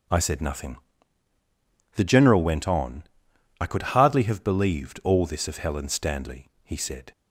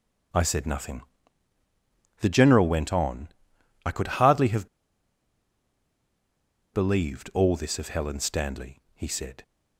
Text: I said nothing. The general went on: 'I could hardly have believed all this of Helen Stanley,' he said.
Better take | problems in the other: first | starts louder than the rest; until 2.5 s; 6 dB; also in the first // pauses between "have" and "believed"; strong; at 4.6 s; 2.0 s long

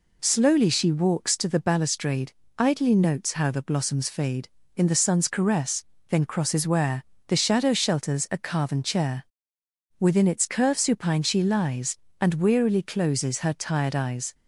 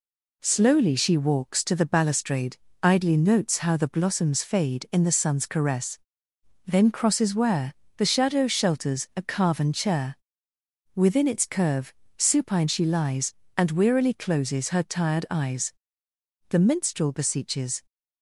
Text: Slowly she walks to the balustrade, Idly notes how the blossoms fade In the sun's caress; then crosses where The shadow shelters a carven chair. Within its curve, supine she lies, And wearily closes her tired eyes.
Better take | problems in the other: first | pauses between "where" and "The"; slight; at 7.7 s; 0.24 s long; slight in the first // goes on to say "The minstrel beseeches"; from 16.4 s on; 1.3 s long

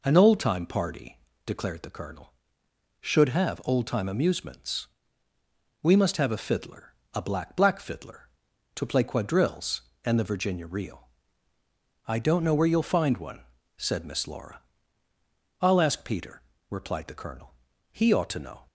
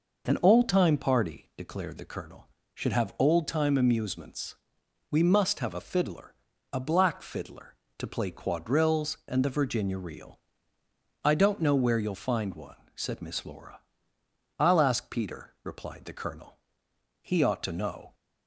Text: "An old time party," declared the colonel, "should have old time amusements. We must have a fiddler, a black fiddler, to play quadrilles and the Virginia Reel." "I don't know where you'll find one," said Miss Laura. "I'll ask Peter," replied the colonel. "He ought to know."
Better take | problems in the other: second | says "black" twice; at 7.5 s

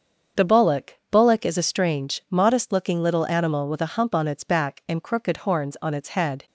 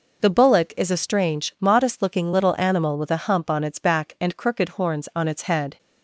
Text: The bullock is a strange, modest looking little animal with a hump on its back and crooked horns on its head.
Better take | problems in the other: second | starts louder than the rest; until 1.5 s; 7 dB // says "bullock" twice; at 1.1 s

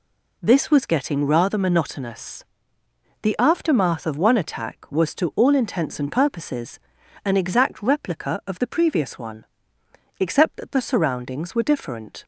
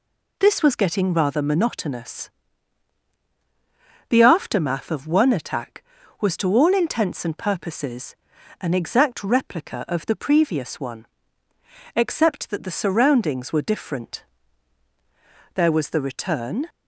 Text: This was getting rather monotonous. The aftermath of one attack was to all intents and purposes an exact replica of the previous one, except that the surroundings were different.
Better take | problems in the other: first | pauses between "purposes" and "an"; at 8.1 s; 0.44 s long; noticeable in the first // goes on to say "There was the return"; noticeable; from 15.5 s on; 1.1 s long

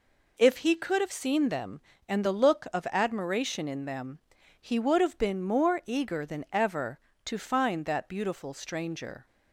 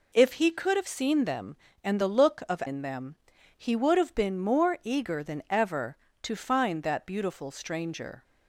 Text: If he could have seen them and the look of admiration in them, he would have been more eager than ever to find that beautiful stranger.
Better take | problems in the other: first | skips "admiration"; at 2.6 s

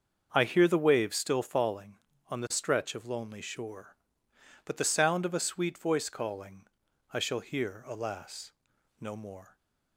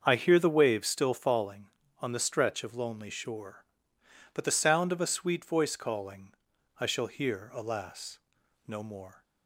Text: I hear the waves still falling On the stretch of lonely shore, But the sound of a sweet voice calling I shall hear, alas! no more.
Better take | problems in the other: neither | starts louder than the rest; the same in both // pauses between "calling" and "I"; noticeable; the same in both

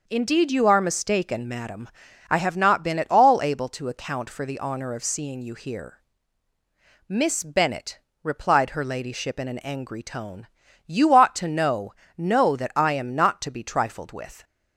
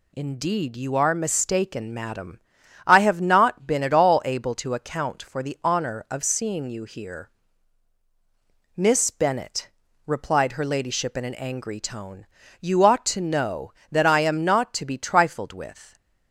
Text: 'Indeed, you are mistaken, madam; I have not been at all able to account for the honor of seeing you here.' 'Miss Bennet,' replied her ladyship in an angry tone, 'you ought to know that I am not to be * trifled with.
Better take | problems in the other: second | says "know" twice; at 12.1 s

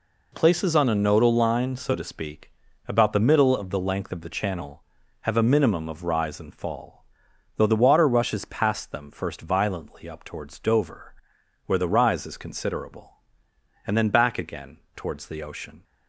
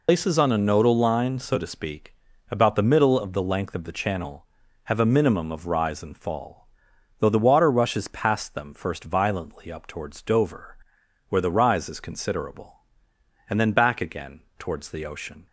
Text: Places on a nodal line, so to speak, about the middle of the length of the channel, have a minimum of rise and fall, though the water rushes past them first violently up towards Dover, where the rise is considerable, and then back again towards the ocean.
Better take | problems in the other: first | loses the start of "Places"; at 0.0 s; 125 ms // pauses between "again" and "towards"; slight; at 14.3 s; 0.18 s long; slight in the first

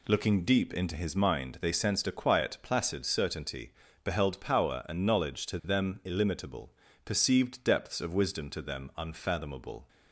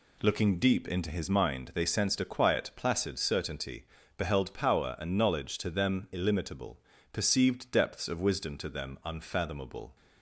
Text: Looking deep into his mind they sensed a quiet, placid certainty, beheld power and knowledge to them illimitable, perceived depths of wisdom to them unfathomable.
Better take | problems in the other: neither | none

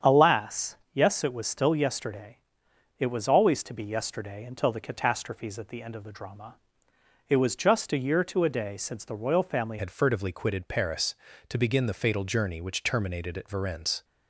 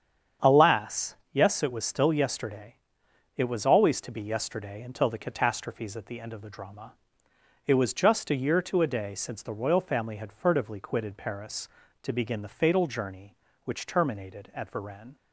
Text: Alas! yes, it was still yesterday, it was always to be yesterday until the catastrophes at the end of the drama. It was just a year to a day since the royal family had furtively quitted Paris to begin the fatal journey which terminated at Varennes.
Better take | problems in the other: second | starts louder than the rest; strong; until 1.2 s; 8 dB; strong in the second // changes voice at "had"; from 9.7 s on; 4.3 s long

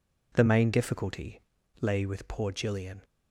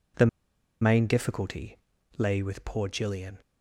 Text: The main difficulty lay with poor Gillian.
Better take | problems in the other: first | pauses between "The" and "main"; noticeable; at 0.2 s; 0.54 s long // pauses between "difficulty" and "lay"; at 1.7 s; 0.42 s long; also in the first

